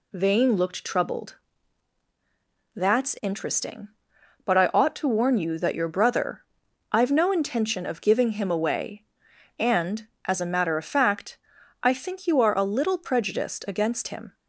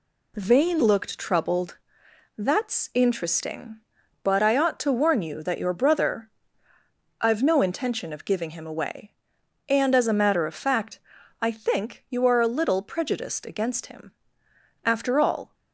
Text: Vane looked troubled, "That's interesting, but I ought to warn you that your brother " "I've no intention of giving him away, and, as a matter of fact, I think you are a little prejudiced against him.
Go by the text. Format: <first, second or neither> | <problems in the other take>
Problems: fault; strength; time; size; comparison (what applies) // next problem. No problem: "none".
first | goes on to say "After all"; noticeable; from 14.8 s on; 0.70 s long